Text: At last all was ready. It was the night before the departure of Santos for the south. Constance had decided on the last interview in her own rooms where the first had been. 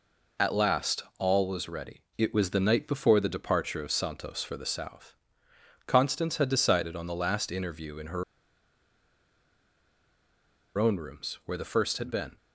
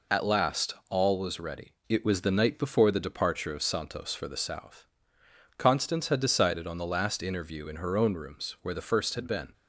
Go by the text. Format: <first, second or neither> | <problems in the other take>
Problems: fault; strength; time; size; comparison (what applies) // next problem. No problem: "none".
second | pauses between "her" and "own"; strong; at 8.2 s; 2.5 s long